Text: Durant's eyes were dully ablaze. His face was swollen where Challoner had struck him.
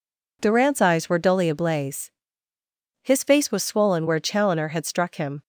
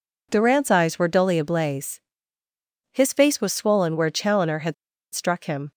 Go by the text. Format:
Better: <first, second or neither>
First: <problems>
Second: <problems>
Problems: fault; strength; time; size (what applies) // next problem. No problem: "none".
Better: first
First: none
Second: pauses between "had" and "struck"; at 4.7 s; 0.40 s long